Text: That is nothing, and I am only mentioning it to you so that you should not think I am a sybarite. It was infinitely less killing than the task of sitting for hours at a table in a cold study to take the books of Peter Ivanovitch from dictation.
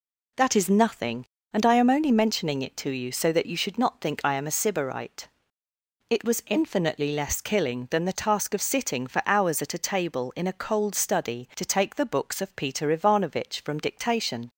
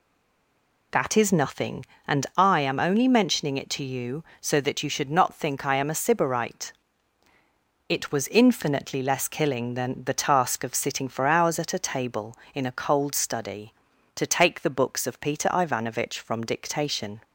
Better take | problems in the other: first | stays silent before the first word; slight; until 0.9 s; 0.9 s long

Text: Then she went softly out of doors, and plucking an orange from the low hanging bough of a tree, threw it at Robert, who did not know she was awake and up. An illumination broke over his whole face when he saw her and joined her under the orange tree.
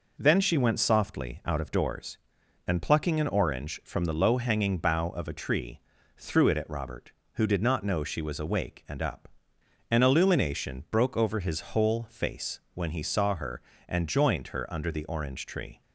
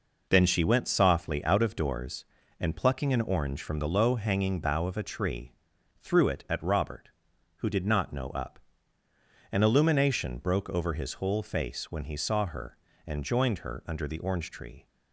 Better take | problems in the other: first | skips "she was awake and"; at 8.2 s

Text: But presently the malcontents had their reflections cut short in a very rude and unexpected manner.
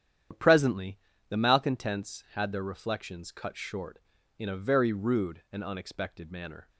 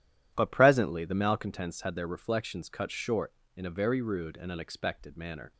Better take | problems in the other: second | loses the start of "But"; at 0.3 s; 75 ms // starts louder than the rest; strong; until 1.6 s; 9.5 dB // pauses between "presently" and "the"; slight; at 0.9 s; 0.32 s long

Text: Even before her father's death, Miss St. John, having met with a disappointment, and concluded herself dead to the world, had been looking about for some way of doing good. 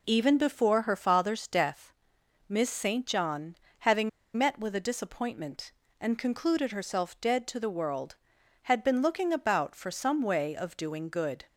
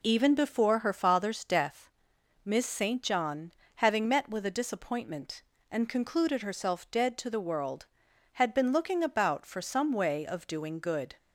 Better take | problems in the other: second | pauses between "having" and "met"; slight; at 4.0 s; 0.26 s long

